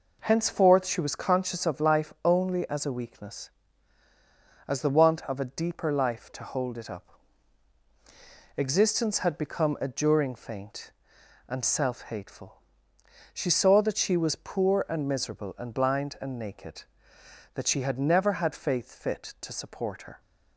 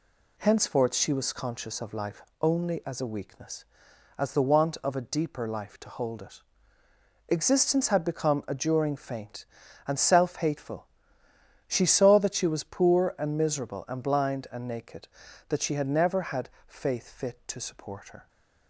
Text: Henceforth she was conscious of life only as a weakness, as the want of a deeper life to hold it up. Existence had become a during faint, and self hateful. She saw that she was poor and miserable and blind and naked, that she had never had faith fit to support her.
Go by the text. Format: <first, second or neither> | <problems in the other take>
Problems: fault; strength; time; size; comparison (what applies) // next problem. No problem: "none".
first | pauses between "life" and "only"; slight; at 2.2 s; 0.20 s long // skips "up"; at 6.8 s // pauses between "had" and "faith"; slight; at 16.4 s; 0.18 s long